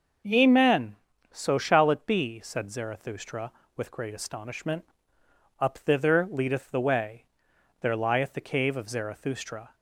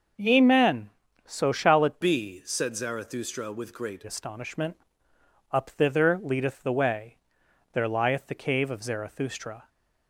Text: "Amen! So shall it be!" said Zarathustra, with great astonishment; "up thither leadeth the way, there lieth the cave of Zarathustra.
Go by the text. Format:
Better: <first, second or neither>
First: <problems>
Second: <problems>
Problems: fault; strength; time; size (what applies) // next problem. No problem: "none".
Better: first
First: none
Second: starts louder than the rest; noticeable; until 1.5 s; 6 dB // changes voice from "be" to "great"; from 2.0 to 4.0 s; 2.0 s long